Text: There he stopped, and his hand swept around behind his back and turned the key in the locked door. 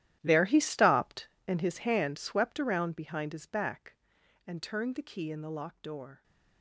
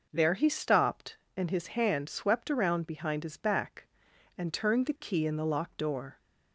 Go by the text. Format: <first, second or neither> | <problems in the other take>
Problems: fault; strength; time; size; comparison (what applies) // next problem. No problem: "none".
second | gets quieter; strong; throughout; 15.5 dB